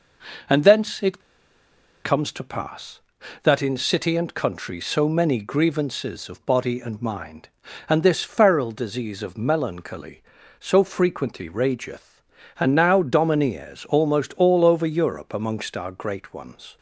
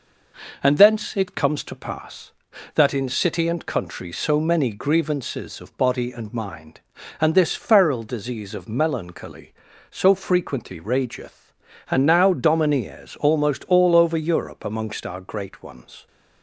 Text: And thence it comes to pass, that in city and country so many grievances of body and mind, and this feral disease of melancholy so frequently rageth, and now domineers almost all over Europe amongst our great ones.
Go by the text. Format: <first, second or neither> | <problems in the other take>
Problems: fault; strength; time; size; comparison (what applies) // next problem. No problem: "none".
second | pauses between "it" and "comes"; noticeable; at 1.2 s; 0.83 s long